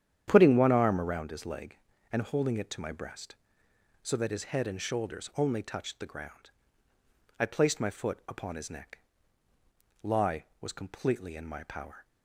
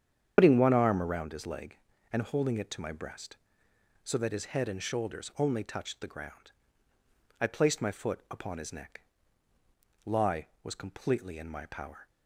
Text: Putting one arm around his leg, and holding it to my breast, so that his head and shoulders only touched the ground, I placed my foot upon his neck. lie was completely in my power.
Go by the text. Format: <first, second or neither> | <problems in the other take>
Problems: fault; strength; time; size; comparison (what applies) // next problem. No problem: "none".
first | loses the start of "Putting"; at 0.3 s; 85 ms // starts louder than the rest; strong; until 1.3 s; 8 dB; strong in the first